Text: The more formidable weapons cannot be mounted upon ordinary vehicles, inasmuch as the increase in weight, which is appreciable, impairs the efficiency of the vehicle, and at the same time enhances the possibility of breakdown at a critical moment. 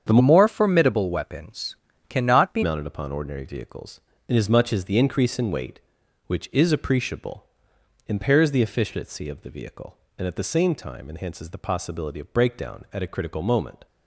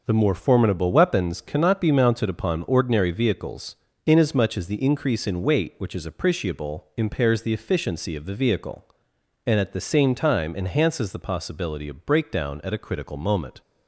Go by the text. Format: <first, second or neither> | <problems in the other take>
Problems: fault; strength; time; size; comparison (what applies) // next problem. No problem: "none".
second | starts louder than the rest; strong; until 1.0 s; 8 dB; noticeable in the second // changes voice from "more" to "be"; from 0.1 to 2.6 s; 2.5 s long // pauses between "weapons" and "cannot"; slight; at 1.7 s; 0.32 s long